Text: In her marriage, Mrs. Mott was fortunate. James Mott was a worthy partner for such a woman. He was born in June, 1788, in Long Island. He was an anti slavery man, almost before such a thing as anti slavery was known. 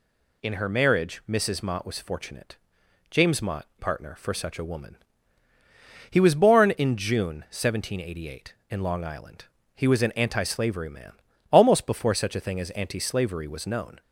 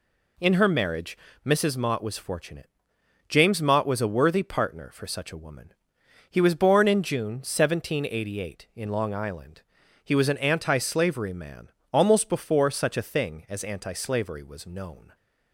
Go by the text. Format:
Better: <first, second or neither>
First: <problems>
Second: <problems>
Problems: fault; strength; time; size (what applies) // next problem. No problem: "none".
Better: second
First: skips "was a worthy"; at 3.7 s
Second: none